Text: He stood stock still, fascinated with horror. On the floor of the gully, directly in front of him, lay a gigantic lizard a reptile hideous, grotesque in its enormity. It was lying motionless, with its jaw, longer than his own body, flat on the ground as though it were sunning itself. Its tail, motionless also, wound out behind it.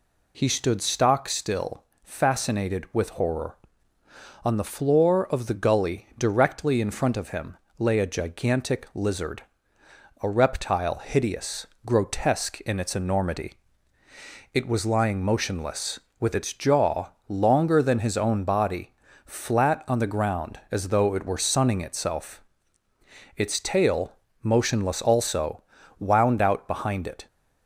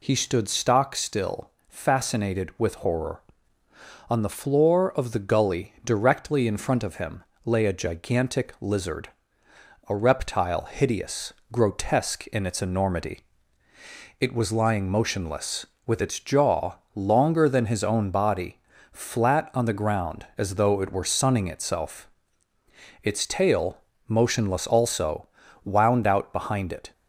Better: neither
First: pauses between "lizard" and "a"; noticeable; at 9.4 s; 0.78 s long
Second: pauses between "lizard" and "a"; noticeable; at 9.0 s; 0.78 s long

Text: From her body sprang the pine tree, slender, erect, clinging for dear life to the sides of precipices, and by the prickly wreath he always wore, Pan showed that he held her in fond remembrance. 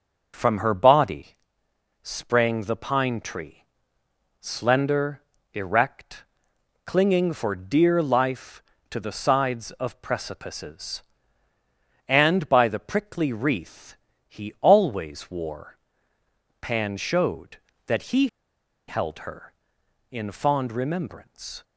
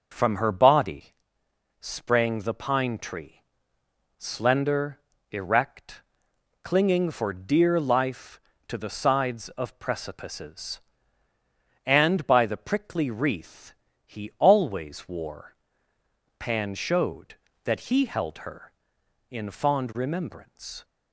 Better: second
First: starts louder than the rest; noticeable; until 1.3 s; 6 dB // pauses between "body" and "sprang"; noticeable; at 1.3 s; 0.66 s long // pauses between "wreath" and "he"; slight; at 13.9 s; 0.32 s long // pauses between "he" and "held"; noticeable; at 18.2 s; 0.61 s long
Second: starts louder than the rest; noticeable; until 1.1 s; 6 dB // pauses between "body" and "sprang"; noticeable; at 1.1 s; 0.66 s long // pauses between "wreath" and "he"; slight; at 13.7 s; 0.32 s long

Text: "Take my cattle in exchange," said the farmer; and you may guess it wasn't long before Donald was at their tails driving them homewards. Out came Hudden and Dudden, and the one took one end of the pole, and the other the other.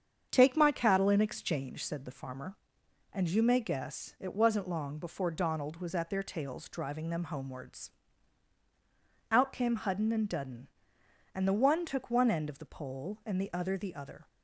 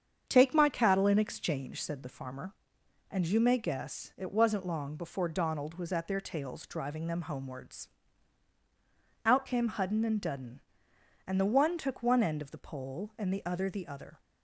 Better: neither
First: starts louder than the rest; strong; until 1.3 s; 7.5 dB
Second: starts louder than the rest; strong; until 1.2 s; 7.5 dB

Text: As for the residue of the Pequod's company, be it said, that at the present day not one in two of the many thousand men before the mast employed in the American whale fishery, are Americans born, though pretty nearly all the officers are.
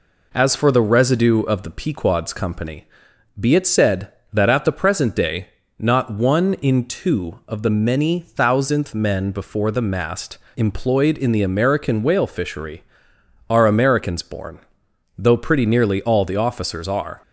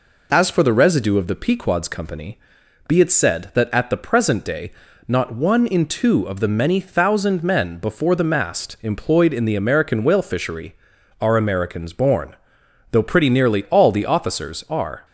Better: second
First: pauses between "day" and "not"; slight; at 5.4 s; 0.32 s long // says "thousandth" for "thousand"; at 8.1 s // pauses between "mast" and "employed"; slight; at 10.3 s; 0.18 s long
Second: pauses between "day" and "not"; slight; at 4.7 s; 0.36 s long

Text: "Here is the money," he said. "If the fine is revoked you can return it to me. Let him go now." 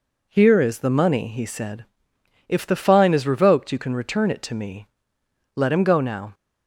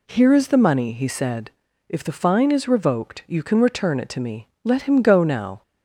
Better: neither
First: none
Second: none

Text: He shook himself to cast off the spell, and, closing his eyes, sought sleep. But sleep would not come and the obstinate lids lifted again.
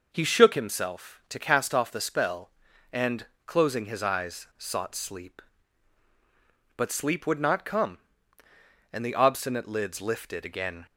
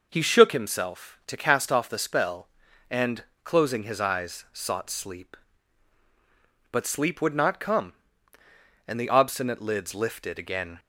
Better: neither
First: none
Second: none

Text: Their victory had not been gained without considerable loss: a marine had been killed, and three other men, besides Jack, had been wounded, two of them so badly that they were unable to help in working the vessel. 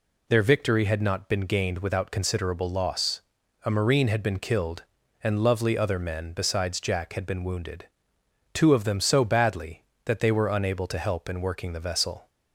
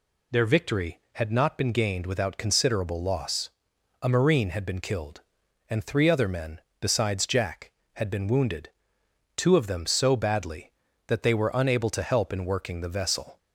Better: second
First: says "lovely" for "three"; at 5.4 s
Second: none

